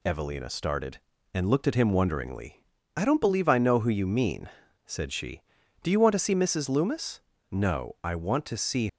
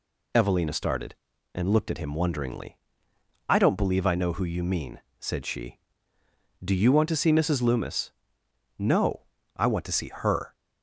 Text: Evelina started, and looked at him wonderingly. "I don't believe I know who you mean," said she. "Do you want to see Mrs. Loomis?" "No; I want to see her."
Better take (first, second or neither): second